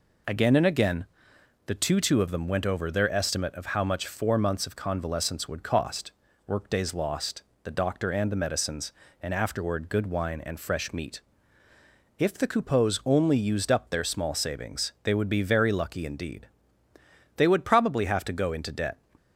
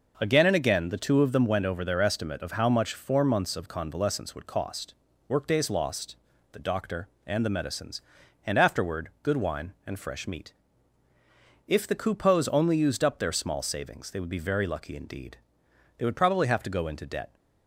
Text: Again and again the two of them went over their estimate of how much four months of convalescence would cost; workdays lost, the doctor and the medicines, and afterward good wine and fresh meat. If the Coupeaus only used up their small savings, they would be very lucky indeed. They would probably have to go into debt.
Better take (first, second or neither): second